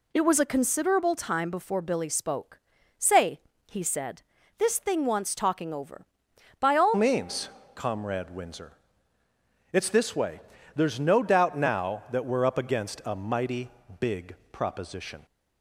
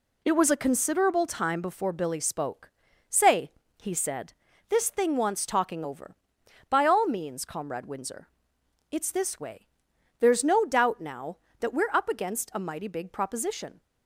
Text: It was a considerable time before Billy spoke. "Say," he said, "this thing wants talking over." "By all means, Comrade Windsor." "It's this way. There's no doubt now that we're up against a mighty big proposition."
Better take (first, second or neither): second